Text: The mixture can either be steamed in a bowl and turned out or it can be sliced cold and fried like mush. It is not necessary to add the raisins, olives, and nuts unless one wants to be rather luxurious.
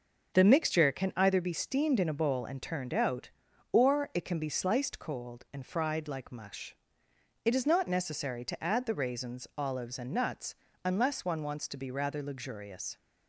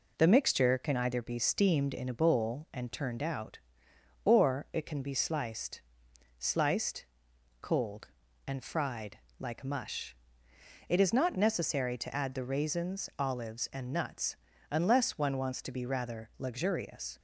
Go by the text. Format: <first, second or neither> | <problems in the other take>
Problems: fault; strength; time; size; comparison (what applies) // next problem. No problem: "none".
first | says "sliced" twice; at 6.3 s // pauses between "fried" and "like"; slight; at 9.1 s; 0.20 s long // pauses between "nuts" and "unless"; slight; at 14.3 s; 0.34 s long; slight in the first